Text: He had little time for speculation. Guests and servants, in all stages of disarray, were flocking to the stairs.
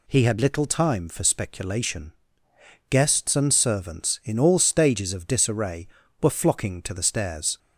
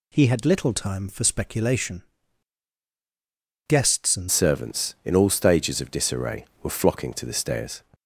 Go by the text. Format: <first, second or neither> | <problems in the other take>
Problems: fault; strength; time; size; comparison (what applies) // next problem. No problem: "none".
first | changes voice at "servants"; from 4.2 s on; 3.6 s long